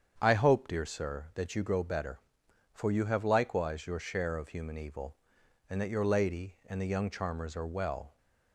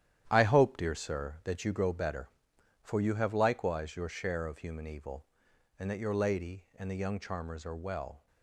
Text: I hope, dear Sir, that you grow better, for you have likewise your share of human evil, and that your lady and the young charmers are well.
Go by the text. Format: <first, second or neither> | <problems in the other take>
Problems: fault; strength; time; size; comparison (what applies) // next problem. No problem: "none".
first | gets quieter; strong; throughout; 9.5 dB // starts louder than the rest; strong; until 1.3 s; 11 dB; strong in the first